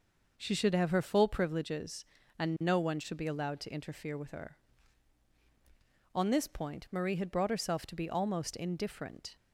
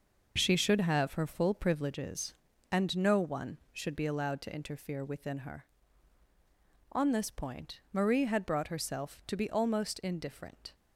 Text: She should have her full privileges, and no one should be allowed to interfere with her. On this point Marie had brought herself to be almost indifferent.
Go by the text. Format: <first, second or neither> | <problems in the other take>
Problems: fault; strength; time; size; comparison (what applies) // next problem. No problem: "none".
first | says "within" for "with"; at 5.0 s